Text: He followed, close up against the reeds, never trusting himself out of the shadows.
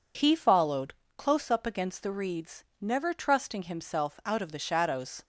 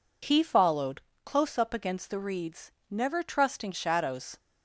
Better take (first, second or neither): first